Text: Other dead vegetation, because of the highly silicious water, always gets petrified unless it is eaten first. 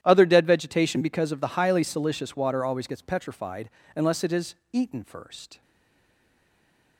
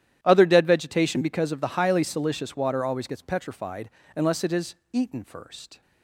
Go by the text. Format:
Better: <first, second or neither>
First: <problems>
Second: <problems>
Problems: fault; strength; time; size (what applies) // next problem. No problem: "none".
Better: second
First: starts louder than the rest; strong; until 1.0 s; 11 dB // pauses between "petrified" and "unless"; slight; at 3.6 s; 0.26 s long // pauses between "is" and "eaten"; slight; at 4.5 s; 0.18 s long // stays silent after the last word; noticeable; from 5.6 s on; 1.3 s long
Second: starts louder than the rest; strong; until 1.2 s; 11 dB // pauses between "petrified" and "unless"; slight; at 3.8 s; 0.26 s long // pauses between "is" and "eaten"; slight; at 4.7 s; 0.18 s long